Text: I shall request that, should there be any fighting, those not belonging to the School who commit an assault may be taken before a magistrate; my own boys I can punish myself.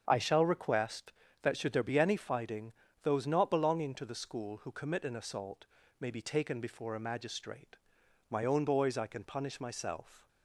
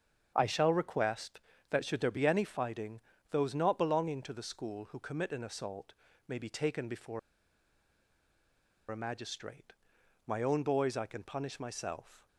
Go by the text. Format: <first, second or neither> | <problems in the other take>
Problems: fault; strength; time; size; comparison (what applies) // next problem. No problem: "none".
first | starts louder than the rest; strong; until 1.3 s; 7.5 dB; strong in the first // pauses between "assault" and "may"; slight; at 5.9 s; 0.32 s long; slight in the first // pauses between "before" and "a"; strong; at 7.1 s; 1.7 s long